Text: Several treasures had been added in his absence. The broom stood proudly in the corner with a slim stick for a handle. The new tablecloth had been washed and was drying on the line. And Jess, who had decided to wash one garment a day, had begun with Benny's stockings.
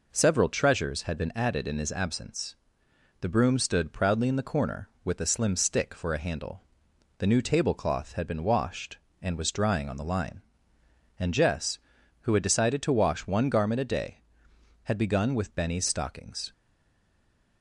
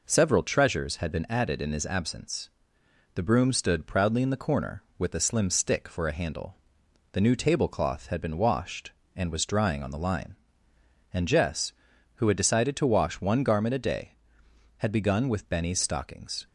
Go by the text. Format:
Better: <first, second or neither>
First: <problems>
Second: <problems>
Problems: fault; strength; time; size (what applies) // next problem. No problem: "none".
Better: second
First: stays silent after the last word; from 16.5 s on; 1.1 s long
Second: none